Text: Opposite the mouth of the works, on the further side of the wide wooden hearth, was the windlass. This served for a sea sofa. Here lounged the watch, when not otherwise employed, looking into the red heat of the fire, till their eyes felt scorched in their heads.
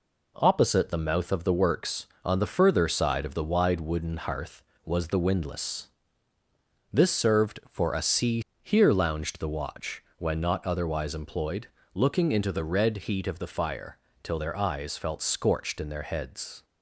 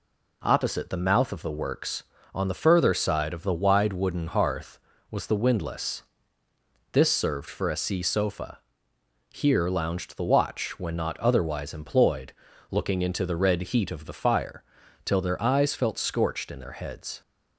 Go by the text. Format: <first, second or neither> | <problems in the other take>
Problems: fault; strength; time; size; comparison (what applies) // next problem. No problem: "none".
second | skips "sofa"; at 8.5 s